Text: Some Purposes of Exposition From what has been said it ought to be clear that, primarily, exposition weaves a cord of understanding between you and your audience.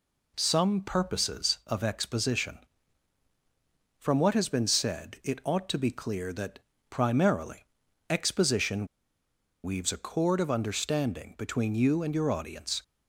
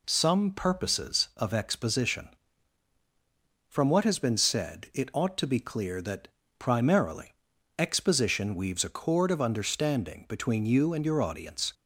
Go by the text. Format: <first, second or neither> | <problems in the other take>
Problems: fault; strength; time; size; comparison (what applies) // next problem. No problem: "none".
second | pauses between "exposition" and "weaves"; noticeable; at 8.8 s; 0.77 s long